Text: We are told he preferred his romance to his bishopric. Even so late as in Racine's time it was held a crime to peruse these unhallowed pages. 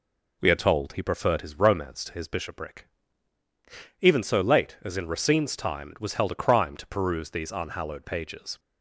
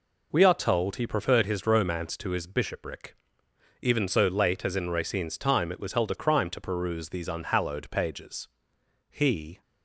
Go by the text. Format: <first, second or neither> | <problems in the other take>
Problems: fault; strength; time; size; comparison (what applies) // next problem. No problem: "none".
first | goes on to say "He"; from 9.0 s on; 0.52 s long